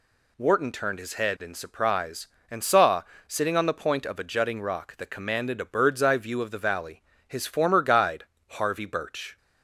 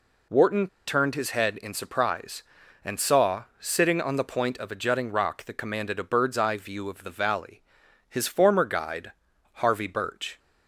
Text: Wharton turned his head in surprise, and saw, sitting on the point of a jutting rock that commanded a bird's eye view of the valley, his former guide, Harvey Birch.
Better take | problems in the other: first | pauses between "Wharton" and "turned"; slight; at 0.6 s; 0.21 s long

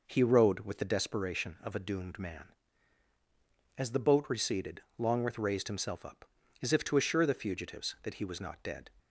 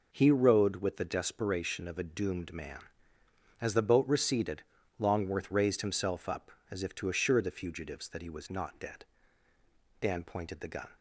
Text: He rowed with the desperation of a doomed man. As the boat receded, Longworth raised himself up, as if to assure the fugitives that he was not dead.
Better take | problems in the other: first | goes on to say "Dan pointed the gun"; noticeable; from 9.9 s on; 0.90 s long

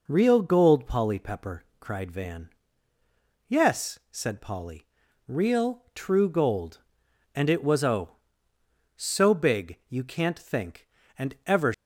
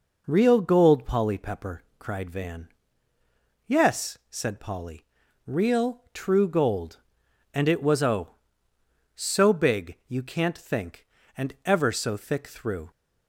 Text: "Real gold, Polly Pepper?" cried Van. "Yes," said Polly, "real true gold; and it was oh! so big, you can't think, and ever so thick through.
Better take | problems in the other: second | stops before "so thick through"; at 11.7 s

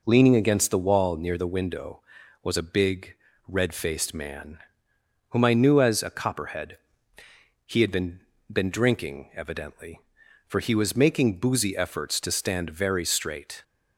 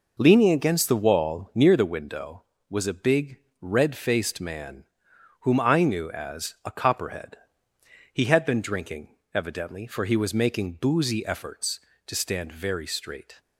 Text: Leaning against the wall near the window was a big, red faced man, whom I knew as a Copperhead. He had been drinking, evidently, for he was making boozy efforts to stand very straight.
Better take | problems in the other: second | says "been" twice; at 8.5 s

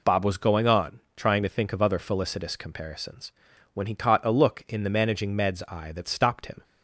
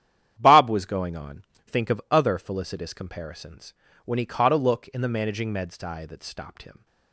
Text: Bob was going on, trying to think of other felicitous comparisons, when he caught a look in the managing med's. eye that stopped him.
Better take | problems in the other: first | starts louder than the rest; strong; until 1.3 s; 10 dB // skips "trying to"; at 1.5 s

